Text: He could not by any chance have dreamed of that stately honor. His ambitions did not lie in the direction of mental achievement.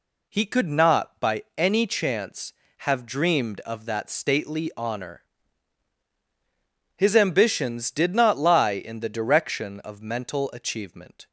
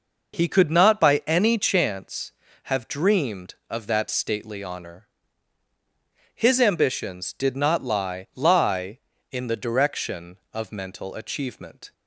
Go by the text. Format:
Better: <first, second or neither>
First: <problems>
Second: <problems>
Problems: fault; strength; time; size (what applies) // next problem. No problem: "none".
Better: first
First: none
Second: says "lie" twice; at 8.3 s